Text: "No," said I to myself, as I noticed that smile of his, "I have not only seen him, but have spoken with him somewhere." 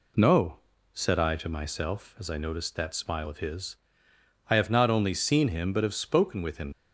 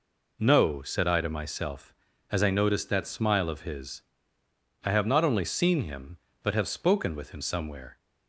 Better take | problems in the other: second | stops before "somewhere"; at 6.7 s

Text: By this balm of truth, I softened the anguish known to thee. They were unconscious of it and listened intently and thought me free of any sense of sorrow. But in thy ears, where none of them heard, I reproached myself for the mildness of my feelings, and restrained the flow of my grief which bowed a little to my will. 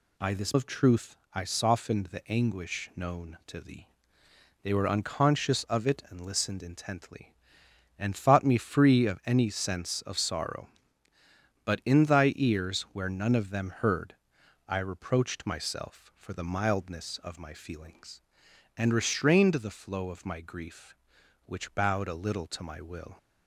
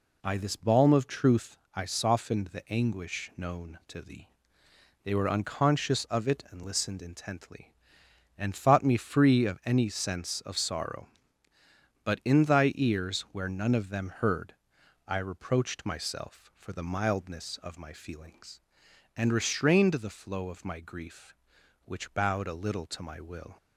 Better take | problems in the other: second | skips "balm"; at 0.5 s

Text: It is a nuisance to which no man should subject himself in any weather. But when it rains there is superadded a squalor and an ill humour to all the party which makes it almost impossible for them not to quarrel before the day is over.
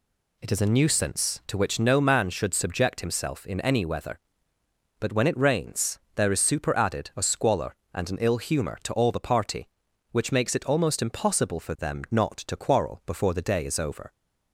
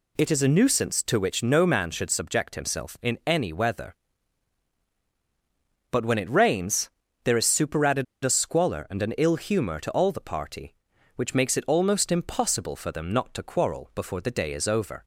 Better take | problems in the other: first | pauses between "rains" and "there"; slight; at 6.9 s; 0.34 s long; slight in the first // pauses between "superadded" and "a"; slight; at 8.0 s; 0.18 s long

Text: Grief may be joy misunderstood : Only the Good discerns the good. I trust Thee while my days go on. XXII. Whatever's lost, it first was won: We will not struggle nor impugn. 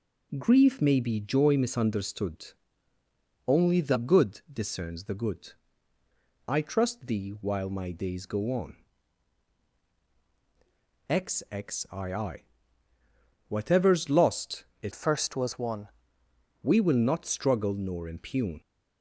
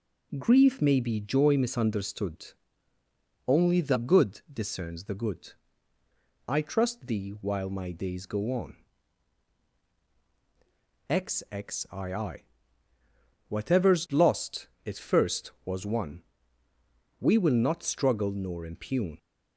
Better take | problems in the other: second | changes voice from "first" to "won"; from 14.9 to 15.8 s; 0.9 s long

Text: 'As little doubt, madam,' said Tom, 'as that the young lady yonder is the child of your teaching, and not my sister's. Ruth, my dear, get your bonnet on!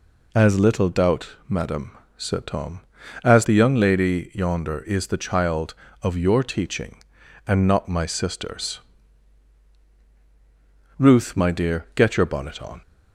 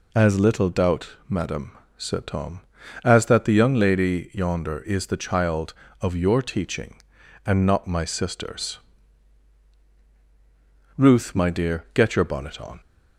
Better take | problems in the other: second | skips "that"; at 3.4 s

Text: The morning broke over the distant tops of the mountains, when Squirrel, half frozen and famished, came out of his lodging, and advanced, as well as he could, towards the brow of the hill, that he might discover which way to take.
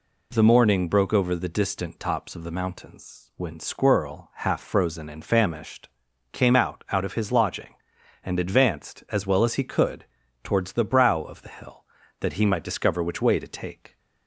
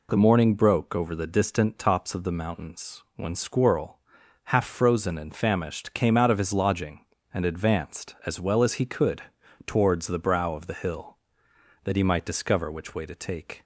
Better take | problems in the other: second | says "out" twice; at 6.8 s

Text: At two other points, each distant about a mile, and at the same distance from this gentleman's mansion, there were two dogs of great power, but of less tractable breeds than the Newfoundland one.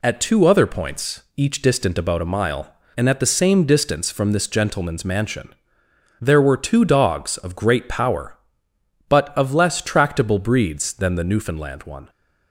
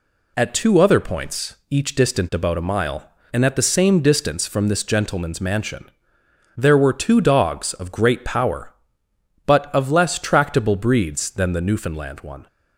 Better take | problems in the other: neither | none

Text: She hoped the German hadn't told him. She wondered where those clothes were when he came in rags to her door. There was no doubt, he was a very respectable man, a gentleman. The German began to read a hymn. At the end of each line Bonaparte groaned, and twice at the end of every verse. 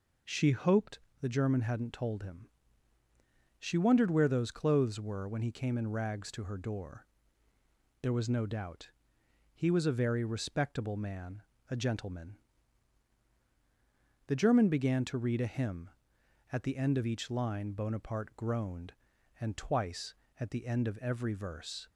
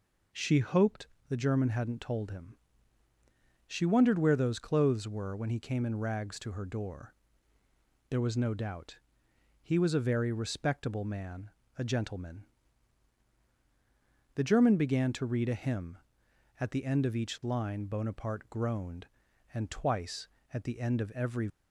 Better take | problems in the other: first | pauses between "hoped" and "the"; slight; at 1.0 s; 0.20 s long; slight in the first // stops before "verse"; at 21.4 s

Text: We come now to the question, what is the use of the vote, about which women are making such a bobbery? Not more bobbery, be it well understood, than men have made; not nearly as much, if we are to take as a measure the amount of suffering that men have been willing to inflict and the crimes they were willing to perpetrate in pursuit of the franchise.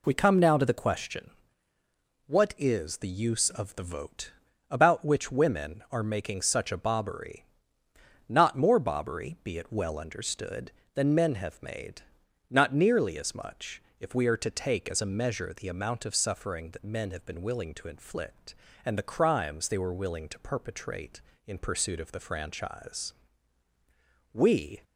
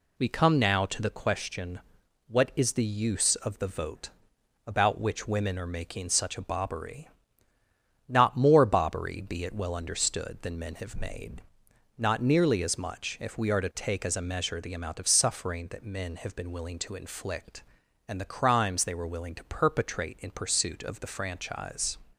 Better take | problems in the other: second | goes on to say "We"; from 24.3 s on; 0.50 s long

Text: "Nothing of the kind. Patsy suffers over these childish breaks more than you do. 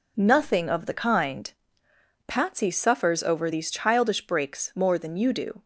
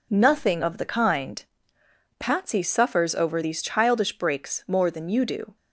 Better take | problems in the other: neither | none

